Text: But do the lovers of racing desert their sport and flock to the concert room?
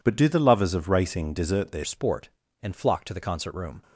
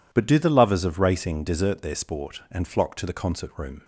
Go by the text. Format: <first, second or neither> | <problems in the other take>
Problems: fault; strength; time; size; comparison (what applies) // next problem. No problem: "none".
second | changes voice at "sport"; from 1.8 s on; 2.0 s long